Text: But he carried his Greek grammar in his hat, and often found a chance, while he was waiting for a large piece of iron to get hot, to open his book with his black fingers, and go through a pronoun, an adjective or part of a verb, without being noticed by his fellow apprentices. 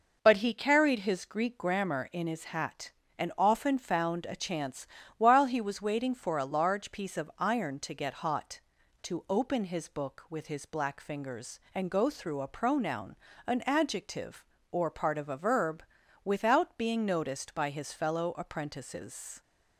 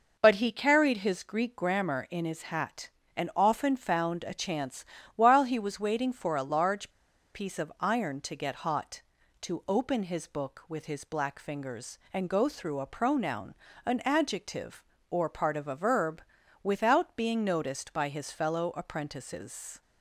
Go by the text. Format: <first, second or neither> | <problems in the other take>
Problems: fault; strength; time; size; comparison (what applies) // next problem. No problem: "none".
first | pauses between "large" and "piece"; at 6.8 s; 0.45 s long